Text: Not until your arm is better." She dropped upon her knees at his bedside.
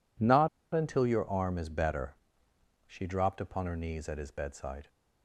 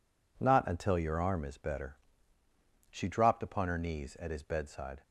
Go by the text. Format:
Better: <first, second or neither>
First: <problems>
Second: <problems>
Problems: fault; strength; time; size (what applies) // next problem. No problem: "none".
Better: second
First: pauses between "Not" and "until"; slight; at 0.4 s; 0.25 s long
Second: none